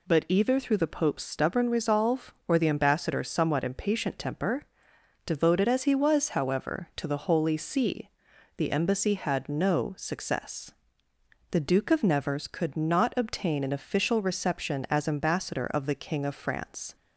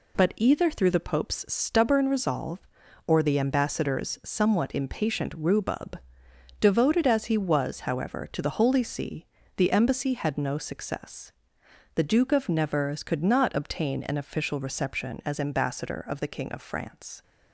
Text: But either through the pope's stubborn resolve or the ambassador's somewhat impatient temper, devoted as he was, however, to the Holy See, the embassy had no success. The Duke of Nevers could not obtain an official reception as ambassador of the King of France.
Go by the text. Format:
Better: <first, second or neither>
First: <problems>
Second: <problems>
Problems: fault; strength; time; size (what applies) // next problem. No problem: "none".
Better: first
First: none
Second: says "rhubub" for "temper"; at 5.3 s